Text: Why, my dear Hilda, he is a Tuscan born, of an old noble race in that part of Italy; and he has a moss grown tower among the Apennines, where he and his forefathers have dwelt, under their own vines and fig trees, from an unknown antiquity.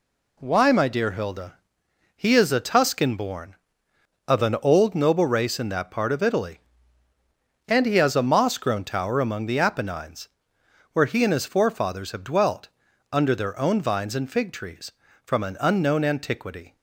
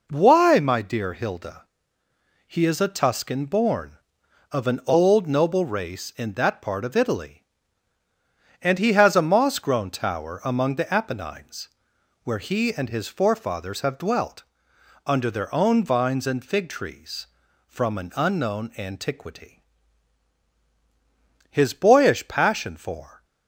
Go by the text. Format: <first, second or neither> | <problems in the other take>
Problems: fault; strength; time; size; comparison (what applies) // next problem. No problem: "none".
first | goes on to say "His boyish passion for"; strong; from 21.5 s on; 1.7 s long